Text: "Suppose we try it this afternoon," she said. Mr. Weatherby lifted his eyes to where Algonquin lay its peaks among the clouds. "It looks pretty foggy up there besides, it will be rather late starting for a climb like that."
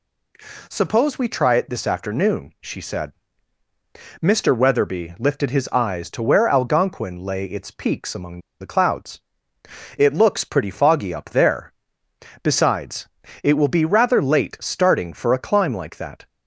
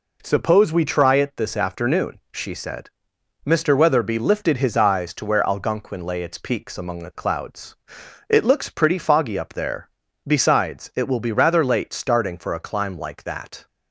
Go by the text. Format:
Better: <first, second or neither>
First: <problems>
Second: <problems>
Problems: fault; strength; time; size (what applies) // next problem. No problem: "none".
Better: second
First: pauses between "among" and "the"; slight; at 8.4 s; 0.19 s long // pauses between "there" and "besides"; noticeable; at 11.7 s; 0.70 s long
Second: pauses between "there" and "besides"; slight; at 9.9 s; 0.36 s long